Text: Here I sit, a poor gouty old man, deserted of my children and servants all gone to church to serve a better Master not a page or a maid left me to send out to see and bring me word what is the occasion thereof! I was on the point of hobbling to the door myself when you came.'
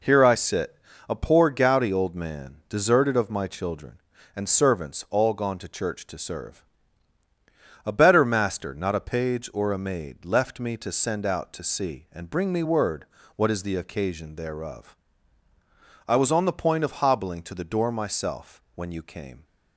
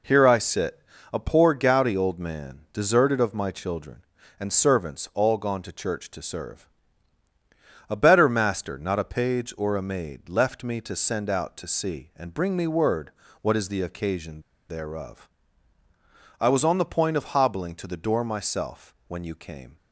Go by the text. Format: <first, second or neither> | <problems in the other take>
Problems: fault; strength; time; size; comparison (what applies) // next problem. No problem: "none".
first | pauses between "serve" and "a"; at 6.6 s; 1.2 s long; also in the first // pauses between "word" and "what"; slight; at 13.1 s; 0.30 s long; slight in the first // pauses between "occasion" and "thereof"; slight; at 14.4 s; 0.28 s long